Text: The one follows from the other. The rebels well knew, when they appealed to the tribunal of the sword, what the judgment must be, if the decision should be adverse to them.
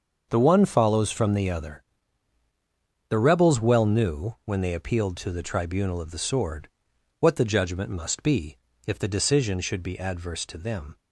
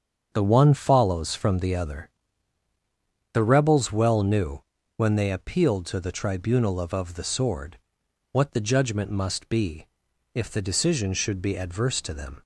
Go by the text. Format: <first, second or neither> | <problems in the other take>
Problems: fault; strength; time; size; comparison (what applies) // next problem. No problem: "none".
first | starts louder than the rest; until 1.3 s; 7 dB; also in the first // says "of" twice; at 6.9 s